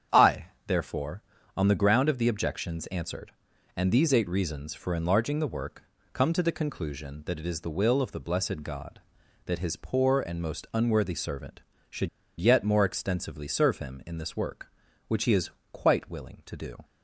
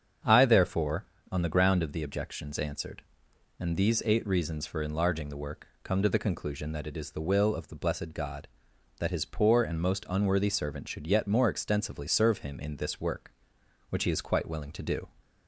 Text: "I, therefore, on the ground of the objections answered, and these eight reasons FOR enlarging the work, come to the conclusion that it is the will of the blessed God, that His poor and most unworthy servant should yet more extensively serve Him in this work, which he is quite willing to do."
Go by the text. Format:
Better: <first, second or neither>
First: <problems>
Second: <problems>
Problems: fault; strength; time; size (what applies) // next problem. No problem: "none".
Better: second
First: starts louder than the rest; strong; until 1.6 s; 8.5 dB // pauses between "should" and "yet"; slight; at 12.0 s; 0.31 s long // pauses between "is" and "quite"; slight; at 15.5 s; 0.22 s long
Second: starts louder than the rest; strong; until 1.5 s; 7.5 dB